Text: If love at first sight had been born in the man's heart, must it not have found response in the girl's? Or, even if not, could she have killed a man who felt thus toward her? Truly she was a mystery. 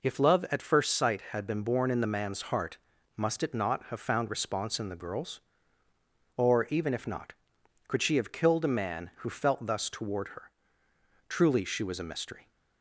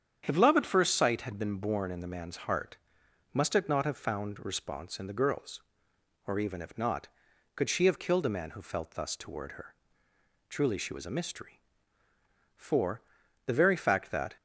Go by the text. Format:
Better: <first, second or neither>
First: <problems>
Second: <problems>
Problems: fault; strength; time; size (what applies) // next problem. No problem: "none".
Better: first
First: none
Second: starts louder than the rest; strong; until 1.2 s; 8.5 dB // goes on to say "For the very fact that"; strong; from 12.5 s on; 1.8 s long